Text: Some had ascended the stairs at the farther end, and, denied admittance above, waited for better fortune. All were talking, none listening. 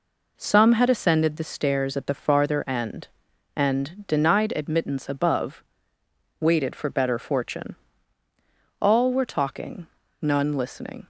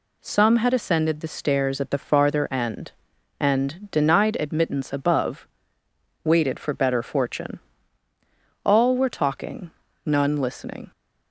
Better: second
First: starts louder than the rest; noticeable; until 1.6 s; 4 dB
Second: none

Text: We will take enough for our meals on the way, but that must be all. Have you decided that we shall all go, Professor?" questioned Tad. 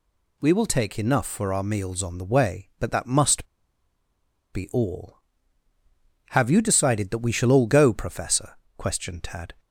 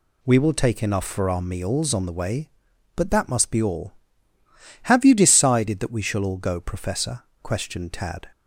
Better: second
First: pauses between "must" and "be"; at 3.4 s; 1.0 s long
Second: none

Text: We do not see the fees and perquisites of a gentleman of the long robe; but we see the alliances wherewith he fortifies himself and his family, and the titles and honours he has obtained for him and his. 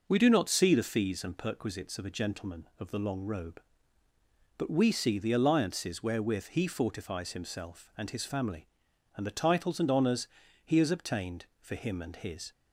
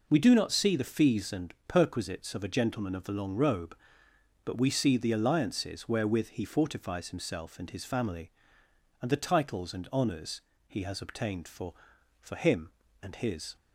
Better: first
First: pauses between "honours" and "he"; slight; at 10.2 s; 0.34 s long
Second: pauses between "honours" and "he"; slight; at 10.4 s; 0.26 s long // says "for" twice; at 12.2 s

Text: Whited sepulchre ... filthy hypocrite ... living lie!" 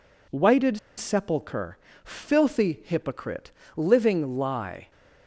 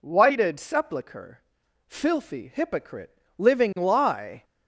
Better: second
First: pauses between "Whited" and "sepulchre"; slight; at 0.7 s; 0.19 s long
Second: none

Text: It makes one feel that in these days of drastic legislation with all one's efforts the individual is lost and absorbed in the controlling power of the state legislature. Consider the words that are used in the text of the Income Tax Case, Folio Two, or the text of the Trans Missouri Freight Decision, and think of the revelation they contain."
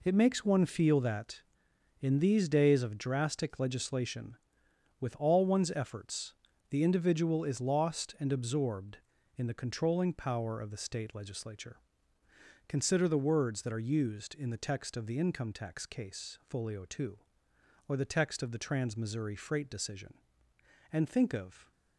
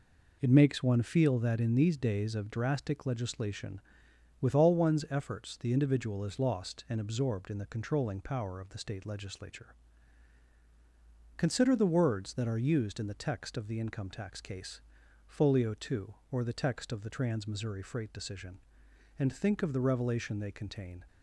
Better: second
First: pauses between "efforts" and "the"; at 6.3 s; 0.38 s long // stops before "the revelation they contain"; at 21.7 s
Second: none

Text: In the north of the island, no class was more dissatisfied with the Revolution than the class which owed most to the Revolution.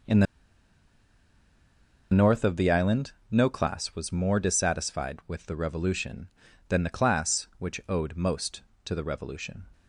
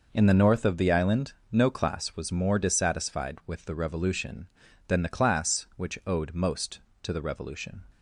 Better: second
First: pauses between "the" and "north"; strong; at 0.2 s; 1.8 s long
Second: none

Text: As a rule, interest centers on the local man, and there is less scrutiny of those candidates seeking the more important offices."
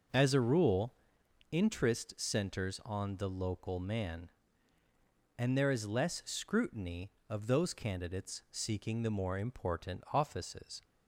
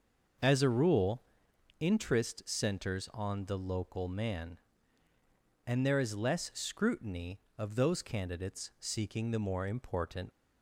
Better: first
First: none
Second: starts louder than the rest; noticeable; until 1.9 s; 6 dB // stops before "offices"; at 10.3 s

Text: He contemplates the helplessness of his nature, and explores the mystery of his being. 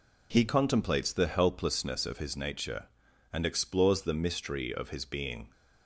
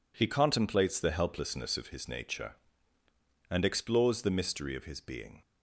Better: neither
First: none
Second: none

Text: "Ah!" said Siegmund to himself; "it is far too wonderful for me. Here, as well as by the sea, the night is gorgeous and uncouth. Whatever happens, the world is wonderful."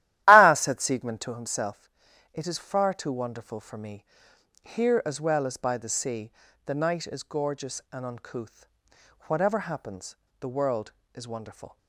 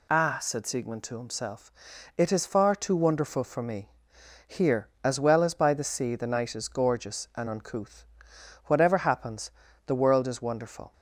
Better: second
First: starts louder than the rest; strong; until 1.5 s; 14 dB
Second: none

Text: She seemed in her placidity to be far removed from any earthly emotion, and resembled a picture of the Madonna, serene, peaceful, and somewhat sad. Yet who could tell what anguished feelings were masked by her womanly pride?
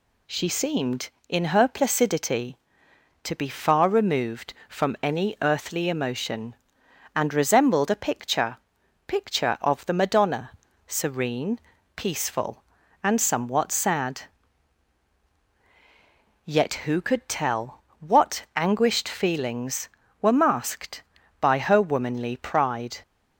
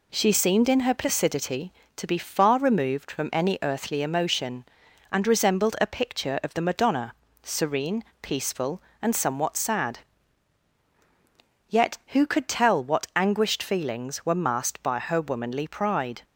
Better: second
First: says "picture" twice; at 9.0 s // pauses between "tell" and "what"; slight; at 17.8 s; 0.20 s long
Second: none

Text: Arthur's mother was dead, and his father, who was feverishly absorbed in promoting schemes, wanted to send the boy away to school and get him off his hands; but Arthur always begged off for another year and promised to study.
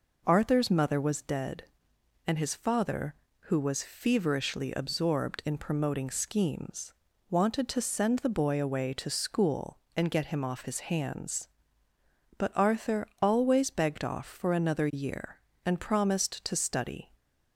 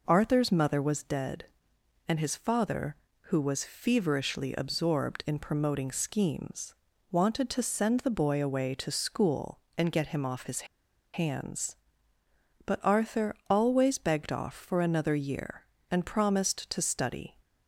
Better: first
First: pauses between "Arthur" and "always"; slight; at 13.0 s; 0.16 s long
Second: pauses between "his" and "hands"; noticeable; at 10.6 s; 0.48 s long // pauses between "Arthur" and "always"; slight; at 13.3 s; 0.16 s long

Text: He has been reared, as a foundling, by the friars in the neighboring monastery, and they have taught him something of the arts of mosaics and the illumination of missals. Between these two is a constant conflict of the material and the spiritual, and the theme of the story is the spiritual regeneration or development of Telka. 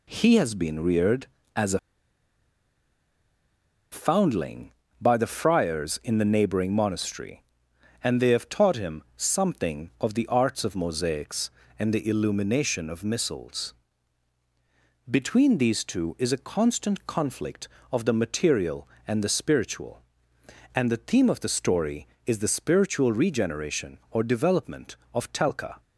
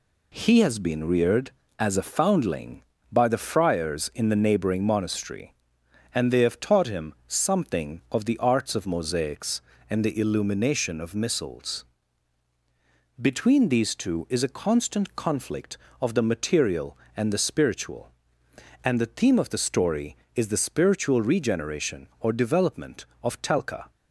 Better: second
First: pauses between "a" and "foundling"; strong; at 1.7 s; 2.1 s long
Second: none

